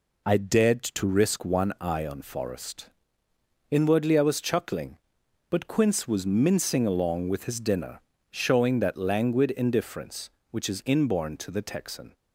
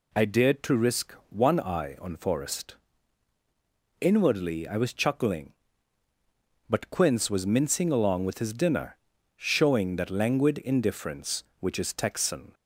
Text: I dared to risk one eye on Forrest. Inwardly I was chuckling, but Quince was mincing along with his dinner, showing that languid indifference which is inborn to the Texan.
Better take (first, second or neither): first